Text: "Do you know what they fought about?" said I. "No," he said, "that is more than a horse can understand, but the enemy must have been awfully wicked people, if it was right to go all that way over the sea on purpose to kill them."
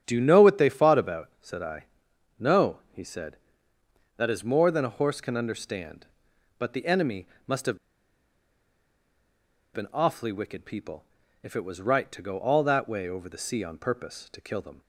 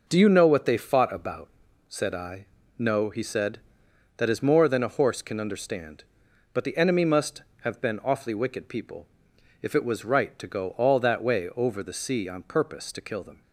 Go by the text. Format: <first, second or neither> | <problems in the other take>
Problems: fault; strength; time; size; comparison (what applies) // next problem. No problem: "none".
second | starts louder than the rest; strong; until 1.0 s; 8.5 dB // pauses between "enemy" and "must"; slight; at 7.2 s; 0.20 s long // pauses between "have" and "been"; strong; at 7.7 s; 1.9 s long